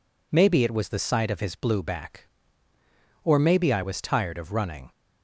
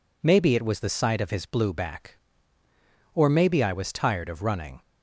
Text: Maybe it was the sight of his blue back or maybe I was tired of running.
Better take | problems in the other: neither | none

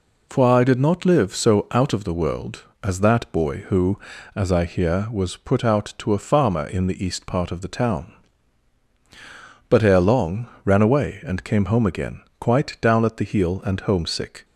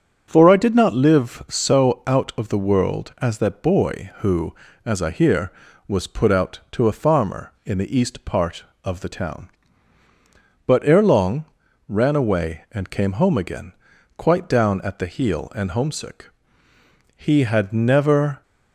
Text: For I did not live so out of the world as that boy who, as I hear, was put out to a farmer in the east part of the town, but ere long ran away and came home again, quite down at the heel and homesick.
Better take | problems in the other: first | starts louder than the rest; strong; until 1.2 s; 7 dB // pauses between "long" and "ran"; at 11.4 s; 0.42 s long; slight in the first // goes on to say "He had never"; noticeable; from 17.1 s on; 1.2 s long

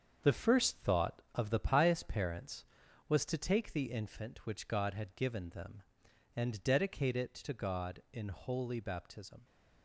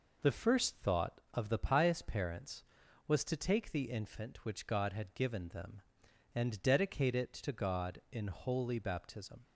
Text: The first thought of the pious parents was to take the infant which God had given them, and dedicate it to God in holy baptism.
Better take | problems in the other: second | gets quieter; strong; throughout; 8 dB

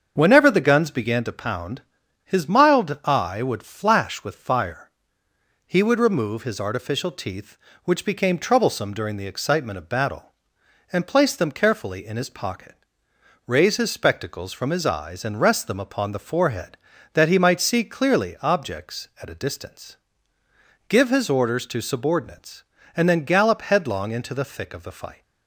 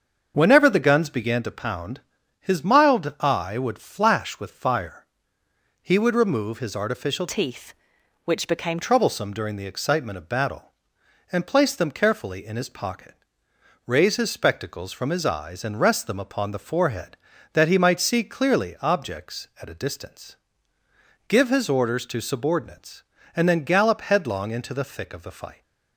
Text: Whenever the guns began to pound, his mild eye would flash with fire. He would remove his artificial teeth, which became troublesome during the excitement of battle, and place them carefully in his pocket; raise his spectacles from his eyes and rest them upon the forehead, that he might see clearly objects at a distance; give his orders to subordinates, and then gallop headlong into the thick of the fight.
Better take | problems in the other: first | starts louder than the rest; until 1.3 s; 6.5 dB; also in the first // changes voice from "teeth" to "became"; from 7.2 to 8.7 s; 1.5 s long

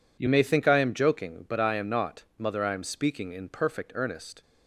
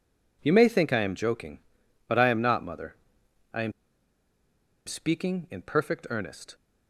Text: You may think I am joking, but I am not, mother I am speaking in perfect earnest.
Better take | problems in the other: first | pauses between "mother" and "I"; noticeable; at 2.9 s; 0.58 s long // pauses between "am" and "speaking"; at 3.7 s; 1.1 s long

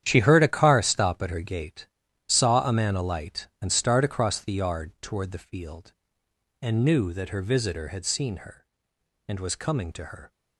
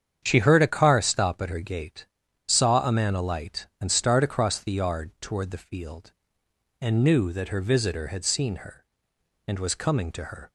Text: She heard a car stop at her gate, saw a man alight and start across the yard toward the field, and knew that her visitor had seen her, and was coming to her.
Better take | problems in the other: second | gets quieter; strong; throughout; 12.5 dB // starts louder than the rest; strong; until 1.0 s; 10 dB; strong in the second

